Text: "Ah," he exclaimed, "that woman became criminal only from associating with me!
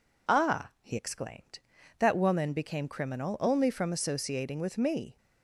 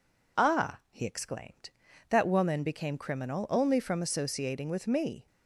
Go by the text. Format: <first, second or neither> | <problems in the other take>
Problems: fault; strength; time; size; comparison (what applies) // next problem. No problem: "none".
neither | none